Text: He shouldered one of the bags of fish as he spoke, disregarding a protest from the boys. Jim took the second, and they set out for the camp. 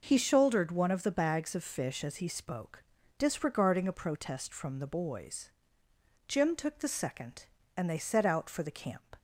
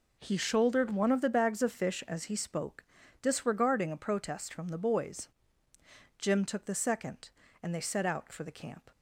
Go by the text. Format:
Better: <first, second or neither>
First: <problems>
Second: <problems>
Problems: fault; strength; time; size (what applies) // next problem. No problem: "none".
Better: neither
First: none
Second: none